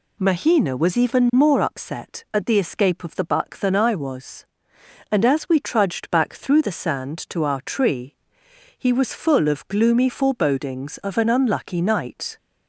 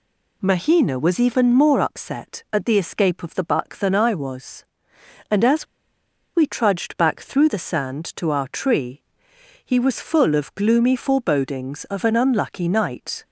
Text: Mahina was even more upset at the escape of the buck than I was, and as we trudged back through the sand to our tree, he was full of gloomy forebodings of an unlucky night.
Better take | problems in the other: first | pauses between "as" and "we"; noticeable; at 5.6 s; 0.69 s long

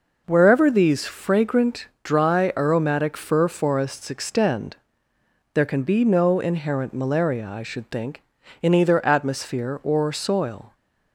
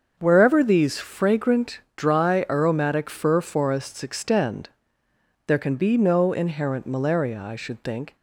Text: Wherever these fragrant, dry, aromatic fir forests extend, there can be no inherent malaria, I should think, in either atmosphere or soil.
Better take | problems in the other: first | starts louder than the rest; until 1.2 s; 6.5 dB // stops before "in either atmosphere or soil"; at 8.1 s

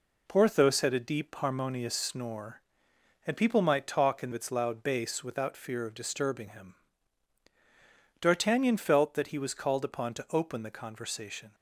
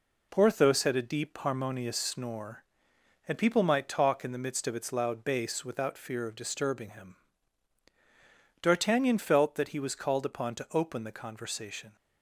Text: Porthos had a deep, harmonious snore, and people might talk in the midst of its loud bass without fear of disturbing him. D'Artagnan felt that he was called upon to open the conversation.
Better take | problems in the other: second | skips "the midst of"; at 4.3 s

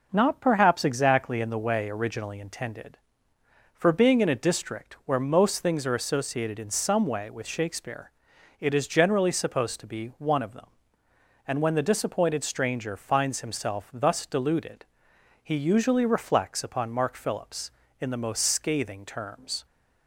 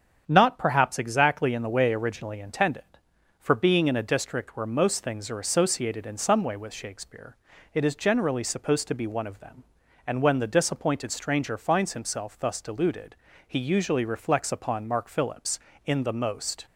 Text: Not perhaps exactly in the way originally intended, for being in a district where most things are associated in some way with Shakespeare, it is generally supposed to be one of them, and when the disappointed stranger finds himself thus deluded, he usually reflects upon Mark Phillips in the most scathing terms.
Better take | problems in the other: first | starts louder than the rest; strong; until 1.2 s; 8 dB // stops before "scathing terms"; at 16.6 s

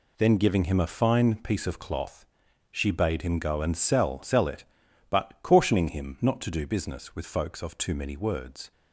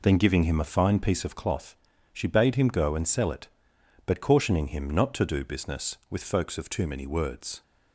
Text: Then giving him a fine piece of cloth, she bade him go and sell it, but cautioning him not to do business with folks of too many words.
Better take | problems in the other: second | says "sell" twice; at 4.2 s

